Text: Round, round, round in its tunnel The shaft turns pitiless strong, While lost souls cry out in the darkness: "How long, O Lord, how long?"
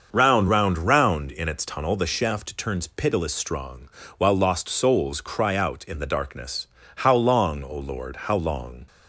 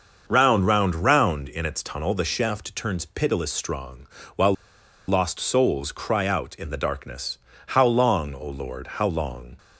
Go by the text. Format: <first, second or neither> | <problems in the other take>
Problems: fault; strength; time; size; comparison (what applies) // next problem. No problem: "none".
first | starts louder than the rest; until 1.2 s; 6.5 dB; also in the first // pauses between "While" and "lost"; noticeable; at 4.5 s; 0.55 s long